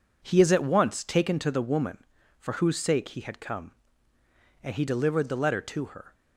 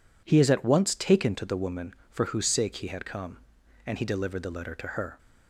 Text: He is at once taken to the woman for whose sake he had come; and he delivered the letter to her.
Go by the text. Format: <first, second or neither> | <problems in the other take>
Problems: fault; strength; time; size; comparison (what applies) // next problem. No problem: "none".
neither | none